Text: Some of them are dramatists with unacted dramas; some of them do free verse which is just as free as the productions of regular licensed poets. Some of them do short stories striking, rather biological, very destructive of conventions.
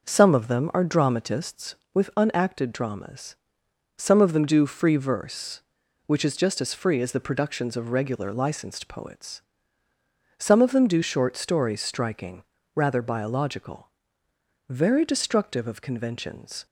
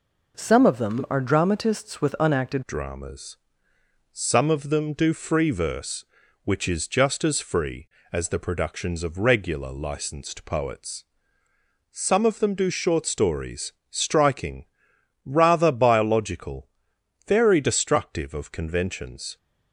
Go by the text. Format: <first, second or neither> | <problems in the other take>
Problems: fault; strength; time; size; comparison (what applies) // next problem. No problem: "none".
first | changes voice at "dramas"; from 2.6 s on; 16.7 s long // pauses between "stories" and "striking"; slight; at 13.7 s; 0.20 s long